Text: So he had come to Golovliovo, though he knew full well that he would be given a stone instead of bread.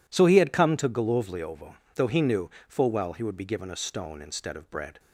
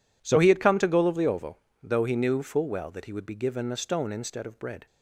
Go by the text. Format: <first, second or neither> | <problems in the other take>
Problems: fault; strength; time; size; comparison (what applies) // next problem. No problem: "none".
second | pauses between "knew" and "full"; slight; at 2.4 s; 0.20 s long // skips "that"; at 3.1 s